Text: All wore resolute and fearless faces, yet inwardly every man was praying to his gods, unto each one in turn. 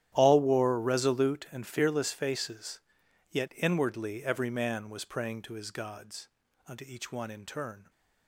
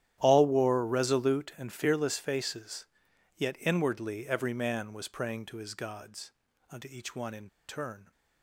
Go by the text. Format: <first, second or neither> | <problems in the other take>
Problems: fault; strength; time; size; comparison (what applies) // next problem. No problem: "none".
first | starts louder than the rest; strong; until 1.2 s; 11.5 dB; strong in the first // pauses between "in" and "turn"; slight; at 7.4 s; 0.20 s long